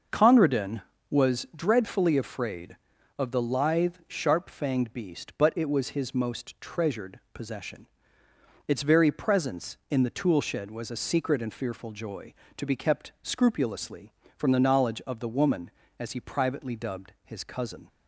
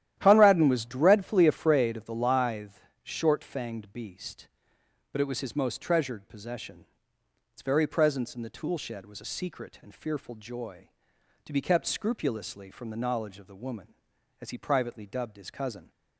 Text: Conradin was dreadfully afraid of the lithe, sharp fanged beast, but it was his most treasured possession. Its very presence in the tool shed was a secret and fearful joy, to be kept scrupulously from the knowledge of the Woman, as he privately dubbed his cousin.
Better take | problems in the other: first | starts louder than the rest; strong; until 1.1 s; 12 dB; also in the first // says "short" for "sharp"; at 3.0 s

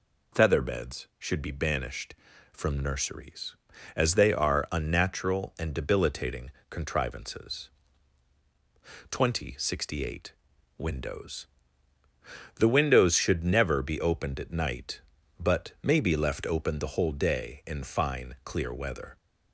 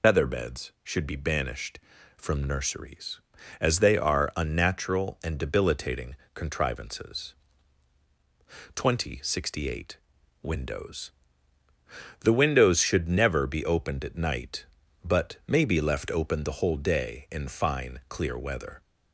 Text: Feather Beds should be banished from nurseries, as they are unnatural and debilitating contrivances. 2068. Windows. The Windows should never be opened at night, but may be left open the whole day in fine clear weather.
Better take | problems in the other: first | loses the start of "Feather"; at 0.0 s; 65 ms // pauses between "debilitating" and "contrivances"; slight; at 6.1 s; 0.22 s long; slight in the first

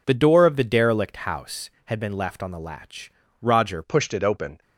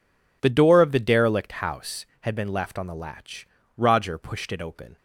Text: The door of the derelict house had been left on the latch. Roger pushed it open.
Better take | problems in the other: second | changes voice at "pushed"; from 3.8 s on; 0.8 s long

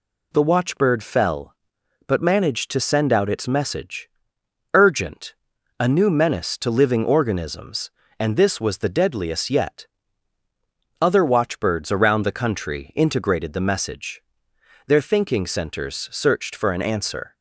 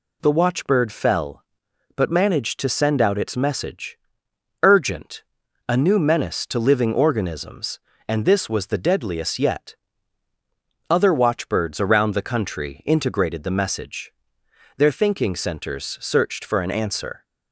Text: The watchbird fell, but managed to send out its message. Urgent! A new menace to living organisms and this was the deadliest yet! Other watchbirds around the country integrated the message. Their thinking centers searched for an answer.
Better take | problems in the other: neither | none

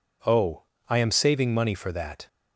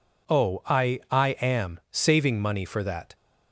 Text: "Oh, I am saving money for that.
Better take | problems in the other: first | says "I" twice; at 1.1 s

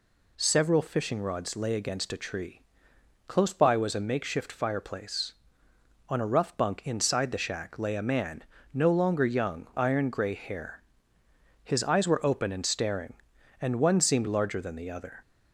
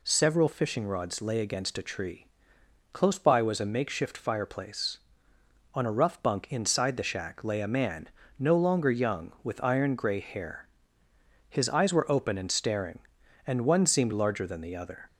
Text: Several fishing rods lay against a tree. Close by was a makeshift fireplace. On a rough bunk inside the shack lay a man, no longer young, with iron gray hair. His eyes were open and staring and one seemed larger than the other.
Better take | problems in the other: second | skips "with"; at 9.7 s

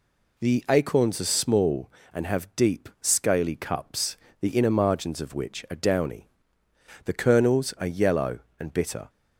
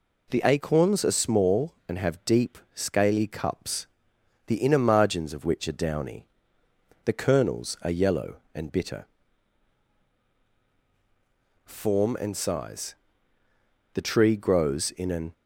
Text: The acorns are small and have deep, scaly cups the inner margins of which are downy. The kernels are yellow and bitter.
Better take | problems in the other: first | pauses between "cups" and "the"; noticeable; at 3.8 s; 0.60 s long; slight in the first // goes on to say "Form and size The tree grows in an"; strong; from 11.6 s on; 3.6 s long

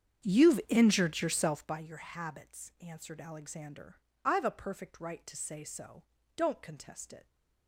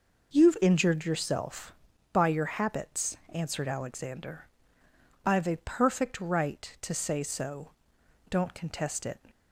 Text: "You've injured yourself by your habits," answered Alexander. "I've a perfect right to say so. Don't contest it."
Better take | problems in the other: second | starts louder than the rest; strong; until 1.8 s; 8 dB

